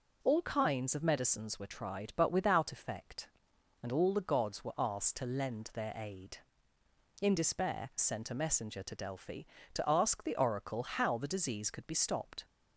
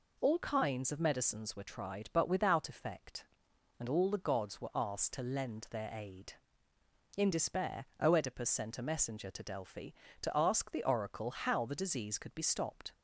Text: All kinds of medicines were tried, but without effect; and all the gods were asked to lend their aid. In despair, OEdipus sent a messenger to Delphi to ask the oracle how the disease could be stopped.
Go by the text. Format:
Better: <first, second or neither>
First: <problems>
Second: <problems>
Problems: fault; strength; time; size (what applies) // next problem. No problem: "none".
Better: second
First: skips "OEdipus"; at 7.9 s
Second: none